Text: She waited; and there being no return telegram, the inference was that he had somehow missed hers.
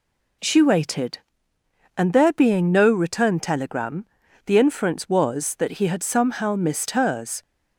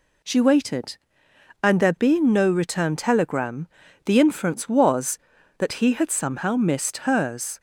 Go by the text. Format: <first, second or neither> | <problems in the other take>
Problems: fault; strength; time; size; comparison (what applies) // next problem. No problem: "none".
neither | none